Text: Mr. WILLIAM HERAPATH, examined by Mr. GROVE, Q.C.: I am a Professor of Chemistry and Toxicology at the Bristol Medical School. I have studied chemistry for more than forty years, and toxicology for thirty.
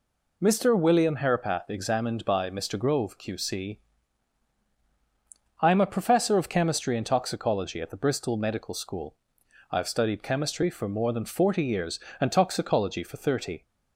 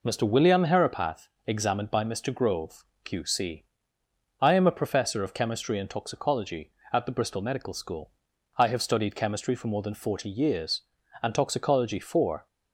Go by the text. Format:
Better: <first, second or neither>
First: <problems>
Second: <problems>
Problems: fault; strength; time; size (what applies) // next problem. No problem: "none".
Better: first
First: none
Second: stops before "thirty"; at 12.4 s